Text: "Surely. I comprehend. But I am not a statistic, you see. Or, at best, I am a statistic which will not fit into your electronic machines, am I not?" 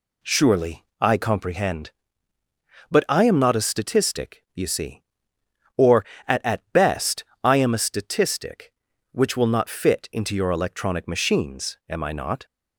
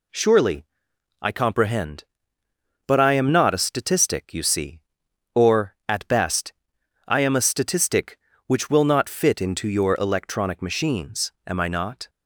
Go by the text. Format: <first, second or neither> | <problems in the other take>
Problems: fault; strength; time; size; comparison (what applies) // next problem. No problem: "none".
second | says "at" twice; at 6.4 s